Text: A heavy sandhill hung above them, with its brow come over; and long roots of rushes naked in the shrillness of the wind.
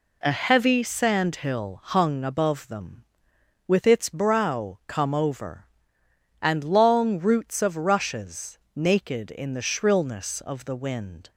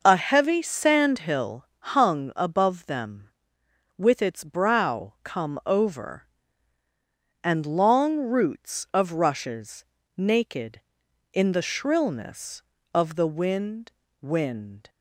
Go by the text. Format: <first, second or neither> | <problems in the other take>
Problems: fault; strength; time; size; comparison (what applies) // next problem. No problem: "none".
first | pauses between "sandhill" and "hung"; slight; at 1.6 s; 0.26 s long // pauses between "rushes" and "naked"; slight; at 9.8 s; 0.32 s long; slight in the first // says "wind" twice; at 14.2 s